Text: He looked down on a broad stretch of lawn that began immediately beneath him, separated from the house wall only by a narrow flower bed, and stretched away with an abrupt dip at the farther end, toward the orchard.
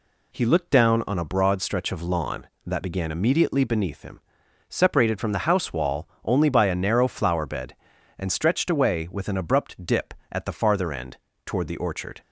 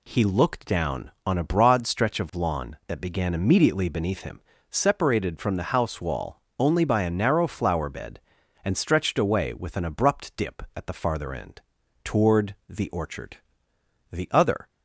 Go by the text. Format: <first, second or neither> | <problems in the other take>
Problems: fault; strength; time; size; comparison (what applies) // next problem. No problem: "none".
first | pauses between "wall" and "only"; slight; at 6.4 s; 0.18 s long; slight in the first // pauses between "toward" and "the"; slight; at 12.5 s; 0.18 s long // goes on to say "The other"; from 14.1 s on; 0.56 s long